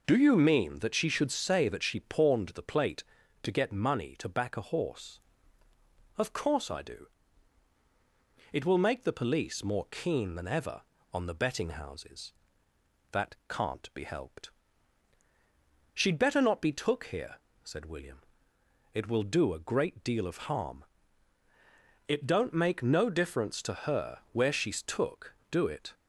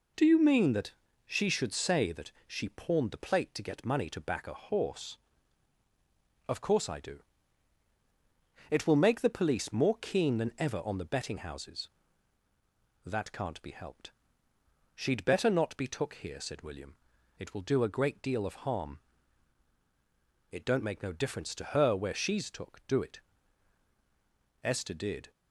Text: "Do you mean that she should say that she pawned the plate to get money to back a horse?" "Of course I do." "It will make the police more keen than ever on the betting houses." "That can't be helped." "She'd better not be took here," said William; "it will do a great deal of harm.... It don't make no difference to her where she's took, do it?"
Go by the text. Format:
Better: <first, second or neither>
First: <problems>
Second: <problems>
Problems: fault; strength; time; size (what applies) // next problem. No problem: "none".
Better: first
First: none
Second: pauses between "that" and "she"; slight; at 0.9 s; 0.34 s long // goes on to say "Esther did"; noticeable; from 24.6 s on; 0.68 s long